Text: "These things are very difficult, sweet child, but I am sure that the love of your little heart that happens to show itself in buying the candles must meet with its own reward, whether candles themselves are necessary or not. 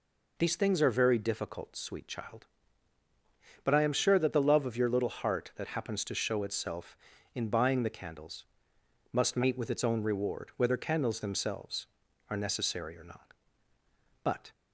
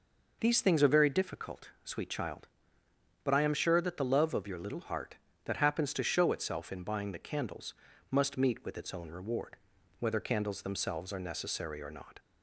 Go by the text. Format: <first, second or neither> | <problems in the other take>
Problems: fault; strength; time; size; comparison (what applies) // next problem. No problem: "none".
second | pauses between "candles" and "must"; noticeable; at 8.4 s; 0.68 s long; also in the second // goes on to say "But"; slight; from 14.2 s on; 0.26 s long